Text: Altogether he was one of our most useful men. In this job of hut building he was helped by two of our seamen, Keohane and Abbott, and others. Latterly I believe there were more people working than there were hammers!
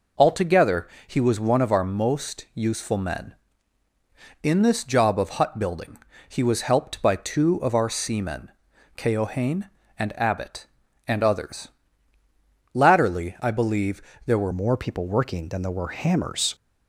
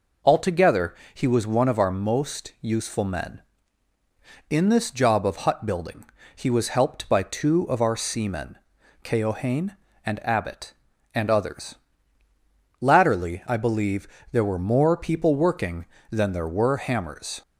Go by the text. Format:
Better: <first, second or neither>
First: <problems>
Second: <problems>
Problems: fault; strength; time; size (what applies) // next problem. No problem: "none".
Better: second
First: pauses between "Altogether" and "he"; slight; at 0.8 s; 0.20 s long // pauses between "building" and "he"; slight; at 5.9 s; 0.30 s long // pauses between "believe" and "there"; slight; at 14.0 s; 0.24 s long // changes voice at "more"; from 14.5 s on; 2.0 s long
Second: pauses between "Altogether" and "he"; slight; at 0.9 s; 0.20 s long // pauses between "building" and "he"; slight; at 6.0 s; 0.30 s long // pauses between "believe" and "there"; slight; at 14.0 s; 0.24 s long